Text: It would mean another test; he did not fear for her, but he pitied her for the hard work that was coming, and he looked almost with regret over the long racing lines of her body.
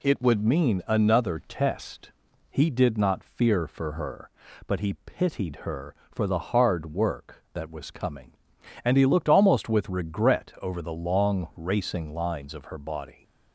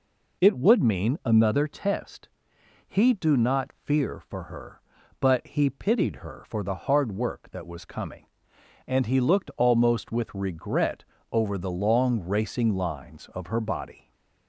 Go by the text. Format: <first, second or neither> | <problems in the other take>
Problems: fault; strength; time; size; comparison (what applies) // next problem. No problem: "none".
first | says "do" for "did"; at 3.1 s // pauses between "regret" and "over"; slight; at 11.0 s; 0.26 s long // stays silent after the last word; slight; from 13.9 s on; 0.5 s long